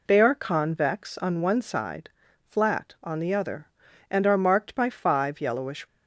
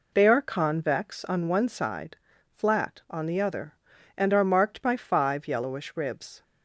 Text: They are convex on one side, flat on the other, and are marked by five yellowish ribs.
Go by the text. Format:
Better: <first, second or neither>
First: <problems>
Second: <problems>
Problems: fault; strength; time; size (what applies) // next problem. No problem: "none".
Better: second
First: stops before "ribs"; at 5.8 s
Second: none